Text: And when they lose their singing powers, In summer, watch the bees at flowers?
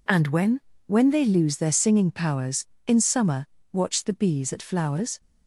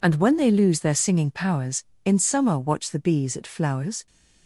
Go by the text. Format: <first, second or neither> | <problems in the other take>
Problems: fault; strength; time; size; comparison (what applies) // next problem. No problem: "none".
second | says "when" twice; at 0.8 s